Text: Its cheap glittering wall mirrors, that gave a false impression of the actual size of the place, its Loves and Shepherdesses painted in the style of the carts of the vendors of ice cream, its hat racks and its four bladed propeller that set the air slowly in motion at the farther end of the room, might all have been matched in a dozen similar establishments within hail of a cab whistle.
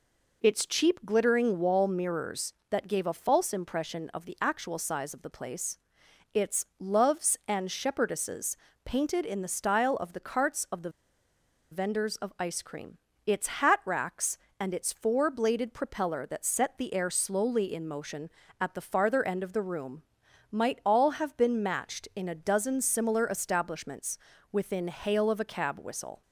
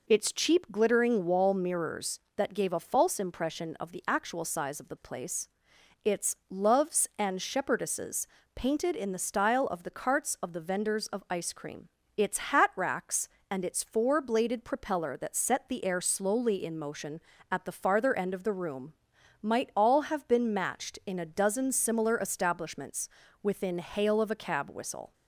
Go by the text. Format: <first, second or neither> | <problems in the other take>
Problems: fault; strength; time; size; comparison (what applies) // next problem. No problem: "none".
second | pauses between "Shepherdesses" and "painted"; slight; at 8.5 s; 0.28 s long; slight in the second // pauses between "the" and "vendors"; noticeable; at 10.8 s; 0.81 s long // pauses between "establishments" and "within"; slight; at 24.1 s; 0.36 s long; slight in the second